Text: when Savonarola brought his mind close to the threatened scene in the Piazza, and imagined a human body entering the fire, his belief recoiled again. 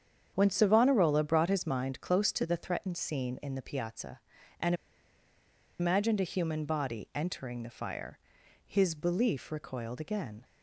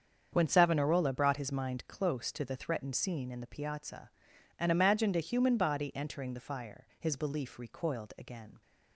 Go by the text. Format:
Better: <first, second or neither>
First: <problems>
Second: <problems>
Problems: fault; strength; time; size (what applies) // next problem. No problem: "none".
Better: second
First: starts louder than the rest; strong; until 1.3 s; 8 dB // pauses between "and" and "imagined"; at 4.7 s; 1.0 s long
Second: starts louder than the rest; strong; until 1.3 s; 7.5 dB